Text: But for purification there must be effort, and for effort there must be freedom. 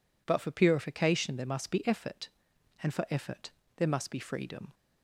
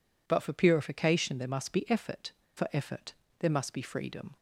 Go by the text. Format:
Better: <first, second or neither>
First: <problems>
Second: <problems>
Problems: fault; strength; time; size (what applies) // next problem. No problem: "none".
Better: first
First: pauses between "effort" and "there"; slight; at 3.5 s; 0.26 s long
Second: skips "and"; at 2.4 s // pauses between "effort" and "there"; slight; at 3.1 s; 0.26 s long